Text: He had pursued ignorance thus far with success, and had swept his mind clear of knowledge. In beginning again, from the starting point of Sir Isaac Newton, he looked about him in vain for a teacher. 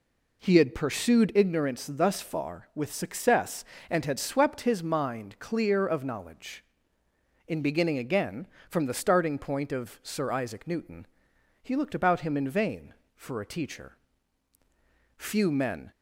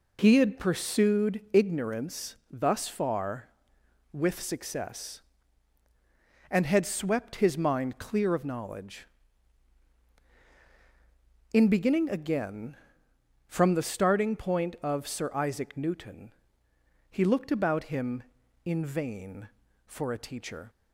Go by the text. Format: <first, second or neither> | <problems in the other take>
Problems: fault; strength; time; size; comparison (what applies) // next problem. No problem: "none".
second | goes on to say "Few men"; noticeable; from 15.1 s on; 0.74 s long